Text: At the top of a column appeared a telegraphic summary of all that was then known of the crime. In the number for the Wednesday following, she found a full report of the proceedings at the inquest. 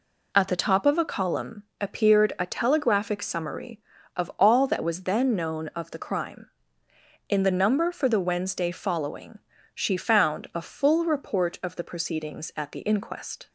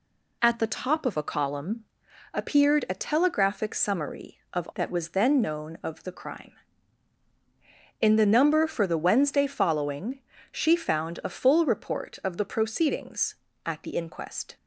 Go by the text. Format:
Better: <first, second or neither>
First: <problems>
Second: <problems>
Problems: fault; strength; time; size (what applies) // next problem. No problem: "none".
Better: first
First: pauses between "column" and "appeared"; slight; at 1.6 s; 0.18 s long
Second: pauses between "column" and "appeared"; noticeable; at 1.8 s; 0.50 s long // skips "all"; at 4.7 s